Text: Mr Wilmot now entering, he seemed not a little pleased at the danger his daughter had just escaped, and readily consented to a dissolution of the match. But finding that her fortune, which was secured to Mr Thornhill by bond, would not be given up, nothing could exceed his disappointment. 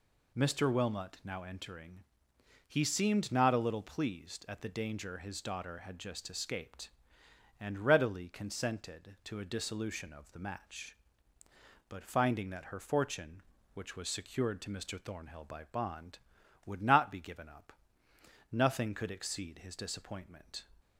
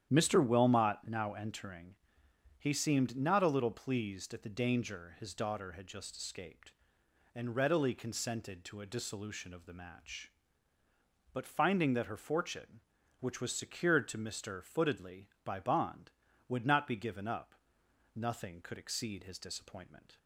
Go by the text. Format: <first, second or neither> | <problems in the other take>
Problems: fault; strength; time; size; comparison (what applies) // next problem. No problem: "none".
first | starts louder than the rest; strong; until 1.2 s; 10 dB // says "Footedly" for "Thornhill"; at 14.6 s